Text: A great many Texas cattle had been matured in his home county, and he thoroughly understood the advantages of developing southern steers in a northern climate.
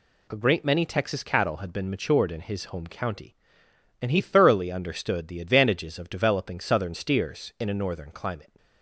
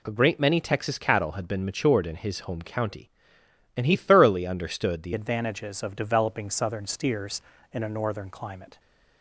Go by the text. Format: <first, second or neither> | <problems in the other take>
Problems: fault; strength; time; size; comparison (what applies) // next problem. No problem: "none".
first | changes voice at "advantages"; from 5.1 s on; 3.6 s long